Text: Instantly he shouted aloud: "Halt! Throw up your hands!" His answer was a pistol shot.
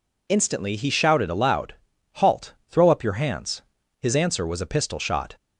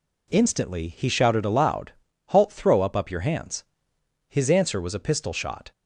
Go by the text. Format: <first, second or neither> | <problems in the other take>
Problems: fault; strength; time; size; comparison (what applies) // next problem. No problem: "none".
first | says "up" twice; at 2.9 s